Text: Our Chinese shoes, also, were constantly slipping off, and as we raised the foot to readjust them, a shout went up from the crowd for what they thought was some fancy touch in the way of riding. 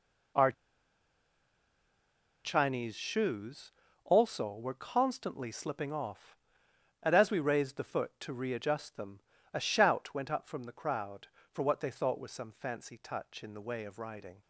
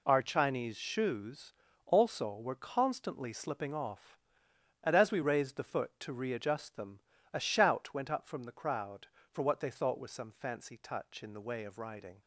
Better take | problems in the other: second | pauses between "Our" and "Chinese"; strong; at 0.5 s; 1.9 s long

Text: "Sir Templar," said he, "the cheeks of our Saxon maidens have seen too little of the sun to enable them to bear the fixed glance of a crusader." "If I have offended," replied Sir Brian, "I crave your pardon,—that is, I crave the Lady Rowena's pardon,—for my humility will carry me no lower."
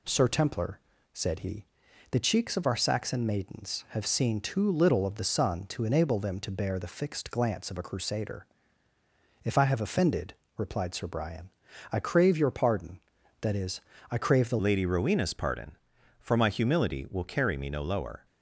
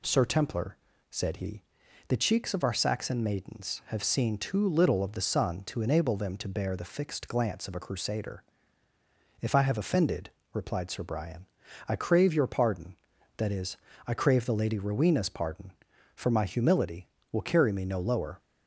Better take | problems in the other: second | changes voice at "Lady"; from 14.5 s on; 3.7 s long

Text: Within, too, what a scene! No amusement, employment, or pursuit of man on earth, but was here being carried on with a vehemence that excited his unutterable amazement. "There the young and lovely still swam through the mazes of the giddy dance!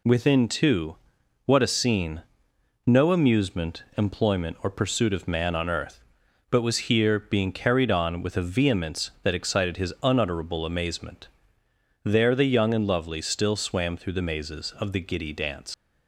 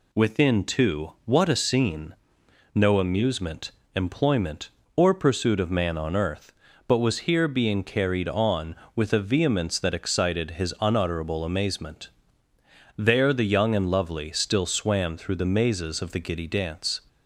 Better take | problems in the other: second | leaves "dance" unfinished; at 15.7 s; 115 ms

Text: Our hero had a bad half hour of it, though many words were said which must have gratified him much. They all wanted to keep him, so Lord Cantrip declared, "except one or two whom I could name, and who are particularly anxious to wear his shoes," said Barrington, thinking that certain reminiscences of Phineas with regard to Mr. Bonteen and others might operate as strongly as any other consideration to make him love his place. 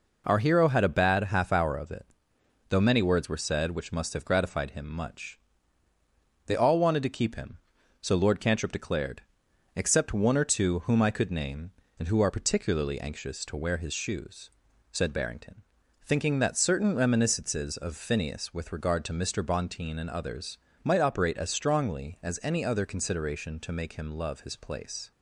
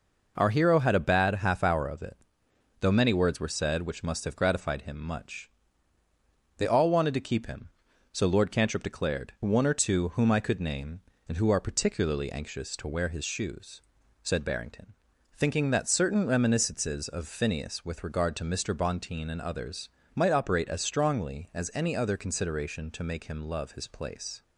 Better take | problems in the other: first | skips "except"; at 9.3 s // pauses between "others" and "might"; slight; at 19.8 s; 0.28 s long; slight in the first

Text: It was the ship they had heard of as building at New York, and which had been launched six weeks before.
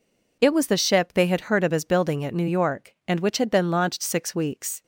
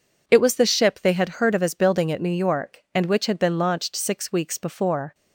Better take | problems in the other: second | stops before "before"; at 4.8 s

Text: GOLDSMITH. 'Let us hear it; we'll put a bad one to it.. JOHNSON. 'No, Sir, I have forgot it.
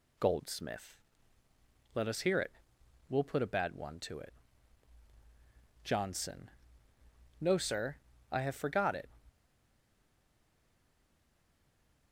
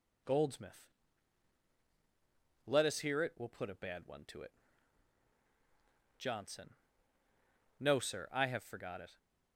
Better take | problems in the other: second | stays silent after the last word; strong; from 9.2 s on; 2.9 s long

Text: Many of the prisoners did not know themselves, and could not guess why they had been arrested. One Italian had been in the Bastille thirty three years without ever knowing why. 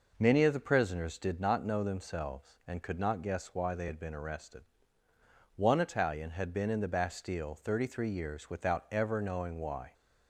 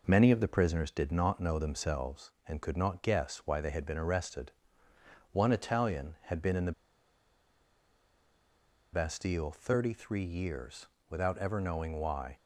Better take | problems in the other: first | pauses between "the" and "Bastille"; strong; at 6.7 s; 2.2 s long // pauses between "years" and "without"; slight; at 10.8 s; 0.24 s long

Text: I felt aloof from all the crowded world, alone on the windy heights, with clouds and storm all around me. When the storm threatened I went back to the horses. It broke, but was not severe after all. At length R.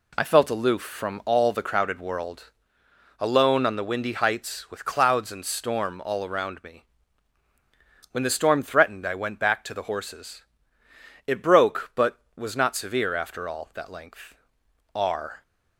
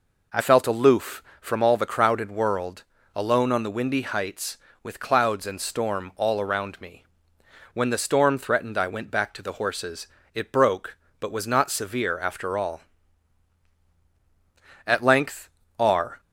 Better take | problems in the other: second | says "That" for "At"; at 13.7 s // pauses between "length" and "R"; noticeable; at 14.3 s; 0.58 s long; slight in the second

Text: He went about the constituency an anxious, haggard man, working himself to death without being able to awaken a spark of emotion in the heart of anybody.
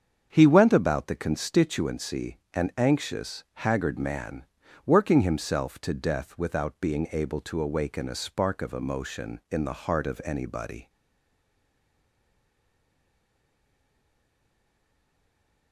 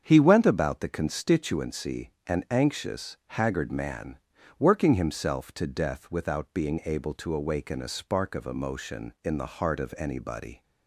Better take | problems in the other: second | starts louder than the rest; strong; until 1.3 s; 7.5 dB; strong in the second // pauses between "constituency" and "an"; slight; at 2.3 s; 0.16 s long; slight in the second // stays silent after the last word; strong; from 10.8 s on; 4.9 s long

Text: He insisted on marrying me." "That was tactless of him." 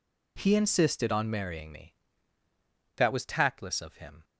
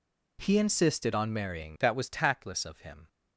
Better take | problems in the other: first | skips "me"; at 1.7 s

